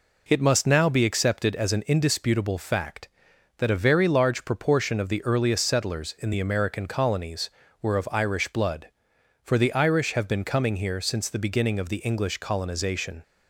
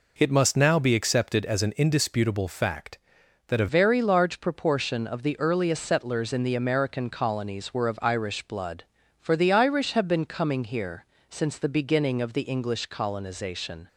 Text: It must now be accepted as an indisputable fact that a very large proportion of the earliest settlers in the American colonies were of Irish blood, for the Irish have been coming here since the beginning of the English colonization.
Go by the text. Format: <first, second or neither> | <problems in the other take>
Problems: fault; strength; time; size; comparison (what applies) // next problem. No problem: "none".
first | changes voice at "very"; from 3.6 s on; 10.2 s long // pauses between "here" and "since"; slight; at 11.0 s; 0.22 s long